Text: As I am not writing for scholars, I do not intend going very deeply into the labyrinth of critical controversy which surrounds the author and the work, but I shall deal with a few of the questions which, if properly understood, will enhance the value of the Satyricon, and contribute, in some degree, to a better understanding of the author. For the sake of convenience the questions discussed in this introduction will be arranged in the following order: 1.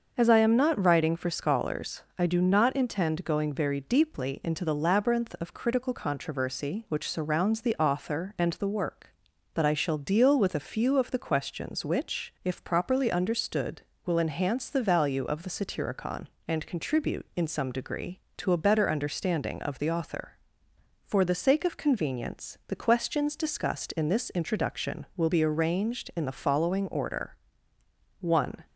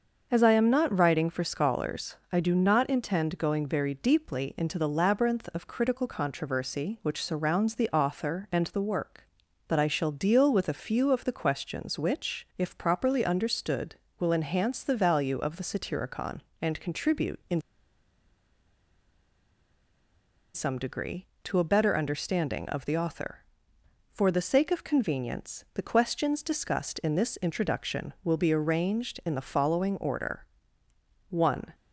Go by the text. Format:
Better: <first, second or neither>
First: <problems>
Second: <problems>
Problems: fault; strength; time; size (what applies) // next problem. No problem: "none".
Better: first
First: starts louder than the rest; until 1.1 s; 6.5 dB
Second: starts louder than the rest; until 1.3 s; 6.5 dB // pauses between "in" and "some"; strong; at 17.5 s; 2.9 s long